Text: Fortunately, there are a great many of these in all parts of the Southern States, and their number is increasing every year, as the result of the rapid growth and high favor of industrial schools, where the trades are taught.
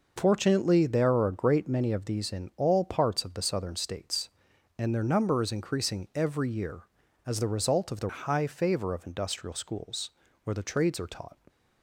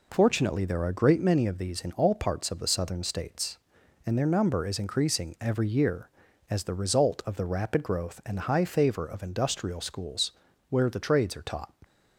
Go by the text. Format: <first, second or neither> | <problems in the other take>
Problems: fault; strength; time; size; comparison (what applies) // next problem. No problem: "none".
second | skips "rapid growth and"; at 8.0 s